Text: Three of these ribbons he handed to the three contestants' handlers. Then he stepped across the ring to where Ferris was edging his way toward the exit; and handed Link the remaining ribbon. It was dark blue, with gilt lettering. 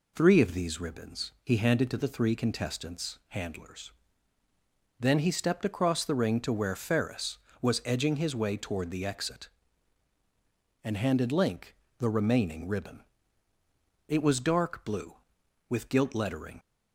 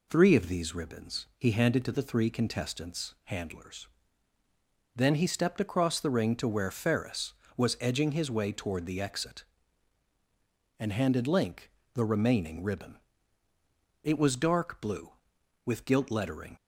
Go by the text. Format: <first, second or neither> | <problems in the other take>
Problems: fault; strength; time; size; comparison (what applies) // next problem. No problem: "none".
neither | pauses between "Link" and "the"; slight; the same in both